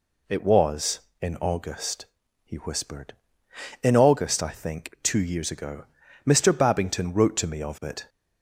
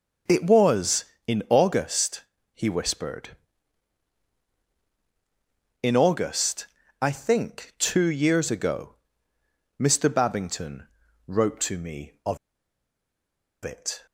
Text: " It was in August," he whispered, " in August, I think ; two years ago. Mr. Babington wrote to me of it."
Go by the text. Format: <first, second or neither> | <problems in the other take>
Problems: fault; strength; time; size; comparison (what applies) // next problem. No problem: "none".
first | pauses between "Babington" and "wrote"; at 10.8 s; 0.40 s long // pauses between "of" and "it"; strong; at 12.3 s; 1.2 s long